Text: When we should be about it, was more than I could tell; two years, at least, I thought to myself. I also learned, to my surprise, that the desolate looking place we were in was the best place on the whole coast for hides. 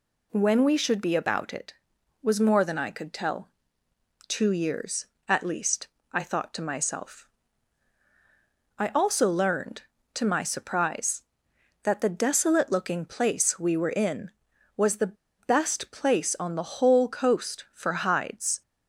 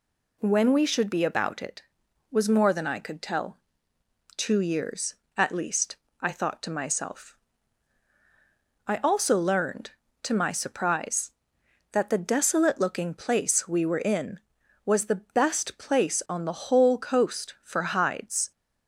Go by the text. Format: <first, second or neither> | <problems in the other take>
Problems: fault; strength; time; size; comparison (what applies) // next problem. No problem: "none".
second | pauses between "the" and "best"; slight; at 15.1 s; 0.24 s long